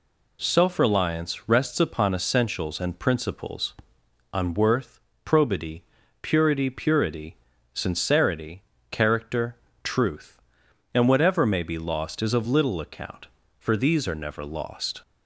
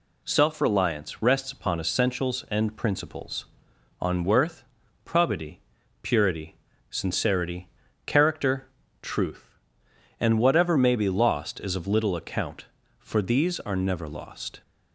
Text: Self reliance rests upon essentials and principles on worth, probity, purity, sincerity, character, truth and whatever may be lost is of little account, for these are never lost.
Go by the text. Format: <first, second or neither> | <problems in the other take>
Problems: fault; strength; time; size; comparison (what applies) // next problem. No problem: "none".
second | says "purity" twice; at 6.7 s